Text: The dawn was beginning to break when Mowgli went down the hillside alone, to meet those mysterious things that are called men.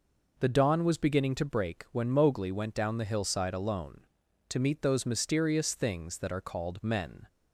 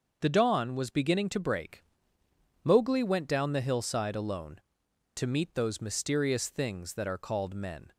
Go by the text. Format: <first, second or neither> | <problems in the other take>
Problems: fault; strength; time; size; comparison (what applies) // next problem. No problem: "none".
first | starts louder than the rest; until 1.2 s; 6.5 dB // skips "when"; at 2.2 s